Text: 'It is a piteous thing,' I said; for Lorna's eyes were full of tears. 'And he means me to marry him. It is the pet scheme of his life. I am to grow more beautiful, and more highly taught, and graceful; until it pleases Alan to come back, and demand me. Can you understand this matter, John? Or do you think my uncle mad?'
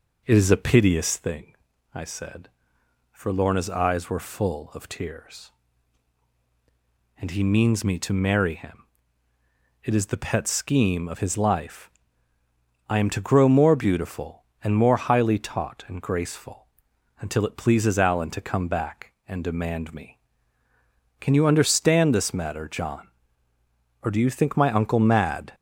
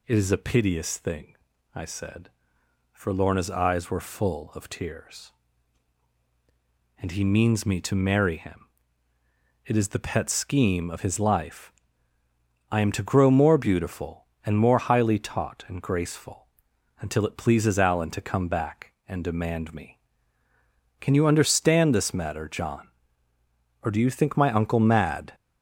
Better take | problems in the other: second | starts louder than the rest; noticeable; until 1.2 s; 5 dB

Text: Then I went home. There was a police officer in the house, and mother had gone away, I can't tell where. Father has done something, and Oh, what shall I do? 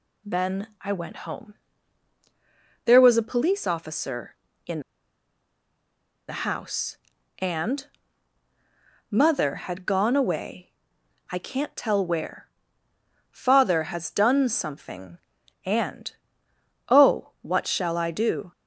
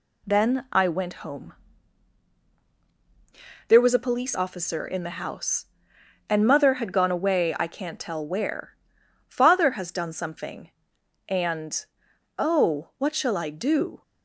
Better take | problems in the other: second | pauses between "in" and "the"; strong; at 4.8 s; 1.4 s long // pauses between "and" and "mother"; at 7.8 s; 1.2 s long // pauses between "and" and "Oh"; noticeable; at 16.1 s; 0.76 s long; noticeable in the second

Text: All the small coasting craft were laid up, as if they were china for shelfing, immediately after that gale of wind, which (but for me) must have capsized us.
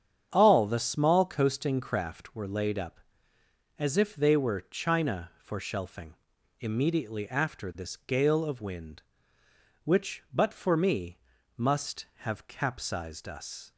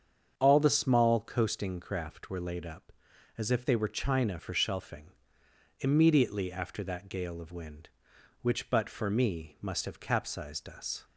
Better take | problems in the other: second | starts louder than the rest; strong; until 1.3 s; 8.5 dB; strong in the second // says "this" for "that"; at 7.7 s

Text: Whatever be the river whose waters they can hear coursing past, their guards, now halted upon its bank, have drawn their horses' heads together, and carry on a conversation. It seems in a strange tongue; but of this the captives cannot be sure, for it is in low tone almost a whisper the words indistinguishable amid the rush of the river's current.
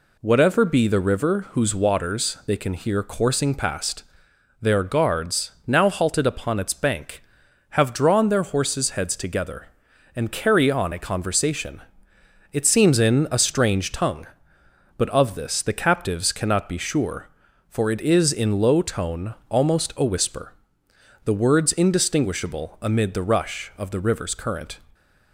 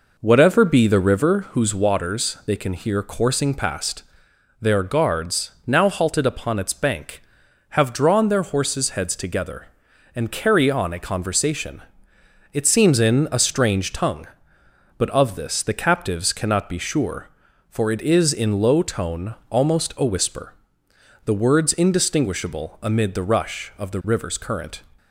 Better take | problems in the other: first | starts louder than the rest; noticeable; until 1.7 s; 4.5 dB // pauses between "tone" and "almost"; slight; at 19.3 s; 0.16 s long; slight in the first // pauses between "whisper" and "the"; noticeable; at 20.5 s; 0.72 s long; noticeable in the first

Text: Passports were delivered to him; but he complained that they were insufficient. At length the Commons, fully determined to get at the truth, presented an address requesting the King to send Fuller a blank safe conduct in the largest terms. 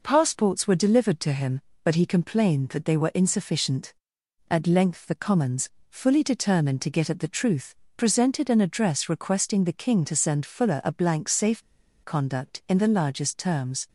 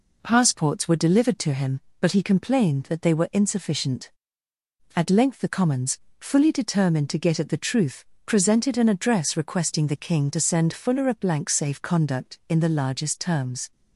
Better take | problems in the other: second | pauses between "safe" and "conduct"; at 11.6 s; 0.41 s long

